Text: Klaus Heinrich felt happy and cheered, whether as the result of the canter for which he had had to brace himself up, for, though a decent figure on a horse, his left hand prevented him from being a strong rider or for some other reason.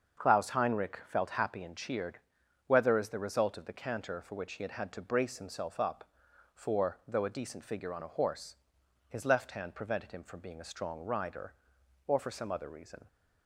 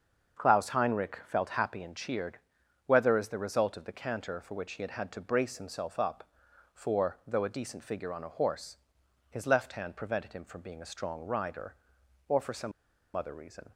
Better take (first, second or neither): first